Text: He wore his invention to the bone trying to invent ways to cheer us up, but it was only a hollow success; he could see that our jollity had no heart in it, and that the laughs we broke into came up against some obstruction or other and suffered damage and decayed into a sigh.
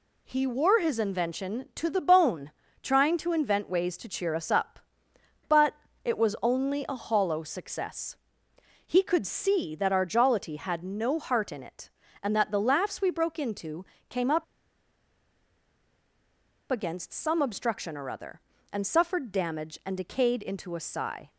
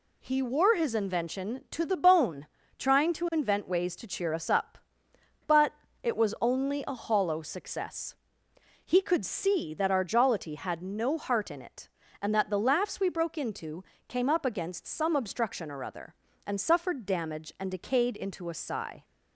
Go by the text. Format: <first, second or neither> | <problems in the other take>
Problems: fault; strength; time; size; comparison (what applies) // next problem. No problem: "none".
second | pauses between "bone" and "trying"; slight; at 2.5 s; 0.30 s long; slight in the second // pauses between "but" and "it"; slight; at 5.7 s; 0.28 s long; slight in the second // pauses between "into" and "came"; slight; at 13.8 s; 0.24 s long; slight in the second // pauses between "up" and "against"; strong; at 14.4 s; 2.2 s long